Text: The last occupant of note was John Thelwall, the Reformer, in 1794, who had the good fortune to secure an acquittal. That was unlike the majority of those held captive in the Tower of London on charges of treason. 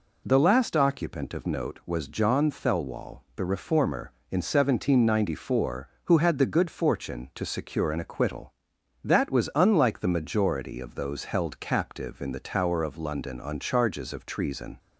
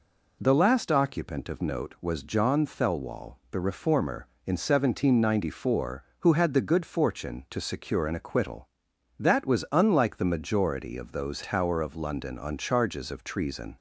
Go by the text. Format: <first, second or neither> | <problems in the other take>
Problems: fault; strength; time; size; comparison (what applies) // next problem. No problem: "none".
first | skips "held captive in the"; at 11.4 s